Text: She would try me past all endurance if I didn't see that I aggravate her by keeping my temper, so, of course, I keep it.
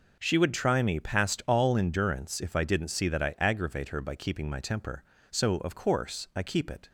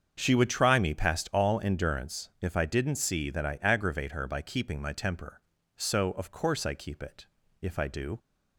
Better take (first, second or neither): first